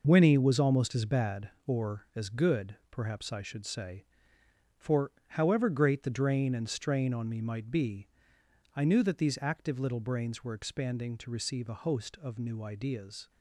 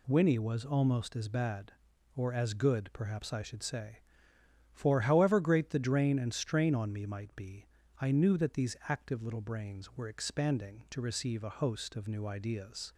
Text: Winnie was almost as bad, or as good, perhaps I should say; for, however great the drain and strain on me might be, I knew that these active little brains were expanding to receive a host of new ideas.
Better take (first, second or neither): second